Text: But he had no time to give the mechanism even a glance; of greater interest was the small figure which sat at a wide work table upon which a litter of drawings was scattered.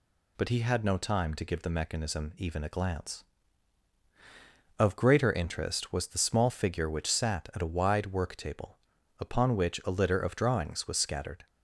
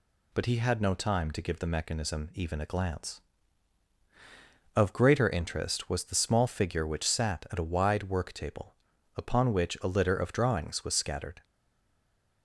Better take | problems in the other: first | pauses between "table" and "upon"; at 8.7 s; 0.42 s long; also in the first // stays silent after the last word; from 11.4 s on; 1.0 s long

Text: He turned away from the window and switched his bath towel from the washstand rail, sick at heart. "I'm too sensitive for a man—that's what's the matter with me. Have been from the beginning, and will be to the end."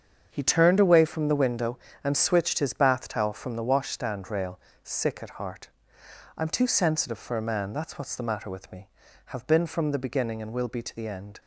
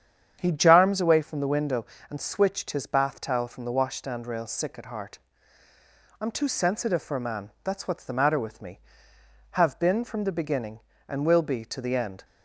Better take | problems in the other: first | starts louder than the rest; strong; until 1.4 s; 8.5 dB; strong in the first // says "jarms" for "turned"; at 0.5 s

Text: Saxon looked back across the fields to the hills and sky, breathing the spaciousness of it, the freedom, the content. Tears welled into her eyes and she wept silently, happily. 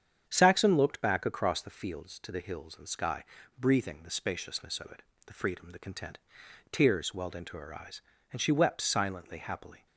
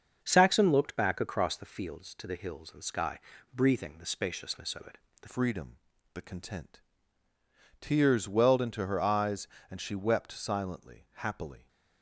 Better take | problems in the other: first | starts louder than the rest; until 1.2 s; 6.5 dB; strong in the first // changes voice at "freedom"; from 5.2 s on; 6.4 s long

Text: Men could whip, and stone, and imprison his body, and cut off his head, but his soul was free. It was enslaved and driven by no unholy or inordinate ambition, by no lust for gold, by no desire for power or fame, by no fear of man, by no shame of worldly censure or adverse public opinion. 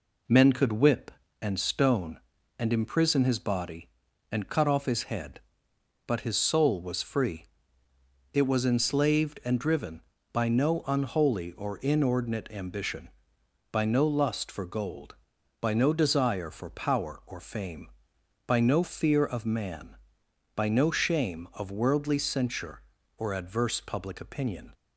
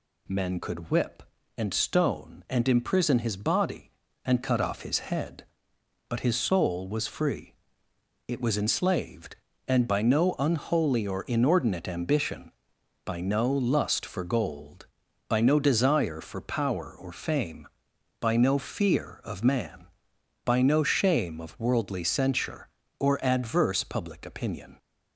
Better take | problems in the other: first | skips "driven"; at 9.8 s

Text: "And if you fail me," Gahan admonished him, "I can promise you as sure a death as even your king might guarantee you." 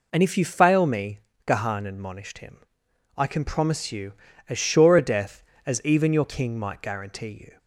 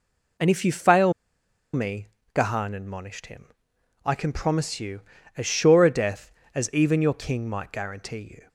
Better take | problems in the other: first | pauses between "fail" and "me"; noticeable; at 1.1 s; 0.61 s long

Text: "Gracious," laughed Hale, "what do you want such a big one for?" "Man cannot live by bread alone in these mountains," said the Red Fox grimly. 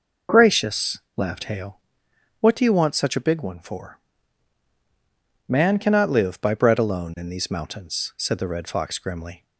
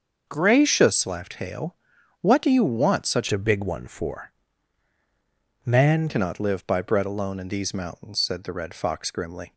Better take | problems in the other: first | starts louder than the rest; until 1.3 s; 6.5 dB // changes voice from "a" to "Man"; from 3.3 to 6.0 s; 2.7 s long

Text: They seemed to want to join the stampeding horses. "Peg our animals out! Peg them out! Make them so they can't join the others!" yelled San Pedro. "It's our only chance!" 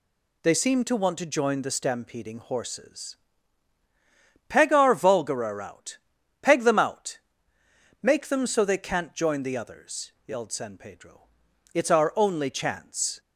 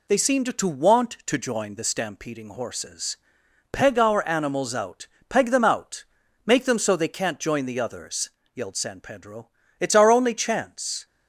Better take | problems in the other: second | says "vulgarer" for "animals"; at 4.9 s

